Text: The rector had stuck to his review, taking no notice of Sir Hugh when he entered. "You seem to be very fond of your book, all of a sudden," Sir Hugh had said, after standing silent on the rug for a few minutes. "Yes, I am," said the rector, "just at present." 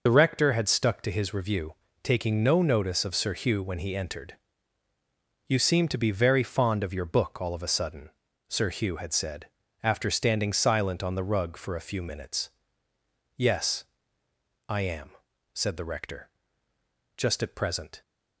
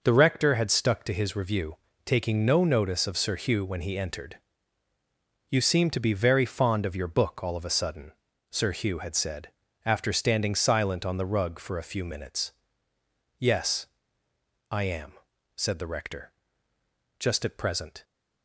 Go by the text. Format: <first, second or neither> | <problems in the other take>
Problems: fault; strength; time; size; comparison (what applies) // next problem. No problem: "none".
second | loses the start of "The"; at 0.0 s; 45 ms